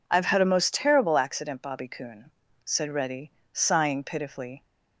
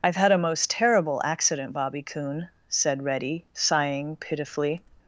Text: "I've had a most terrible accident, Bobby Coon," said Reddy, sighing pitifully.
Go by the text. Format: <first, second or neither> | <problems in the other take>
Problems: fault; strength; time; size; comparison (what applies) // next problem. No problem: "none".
first | loses the start of "I've"; at 0.0 s; 35 ms